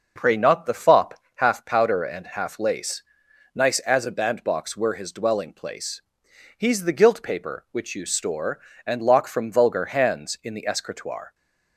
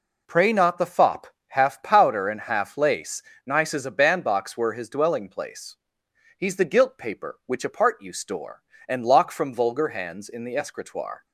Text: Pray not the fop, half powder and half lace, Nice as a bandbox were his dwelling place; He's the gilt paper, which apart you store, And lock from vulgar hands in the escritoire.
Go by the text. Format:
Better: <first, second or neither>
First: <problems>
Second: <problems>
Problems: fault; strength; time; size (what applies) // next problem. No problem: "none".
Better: second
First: skips "apart"; at 7.9 s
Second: none